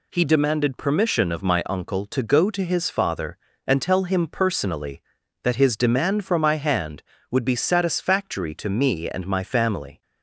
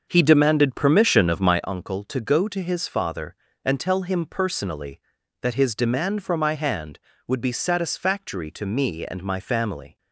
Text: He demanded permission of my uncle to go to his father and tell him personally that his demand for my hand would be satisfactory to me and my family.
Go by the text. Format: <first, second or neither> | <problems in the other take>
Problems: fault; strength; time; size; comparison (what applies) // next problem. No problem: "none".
first | starts louder than the rest; until 1.7 s; 6.5 dB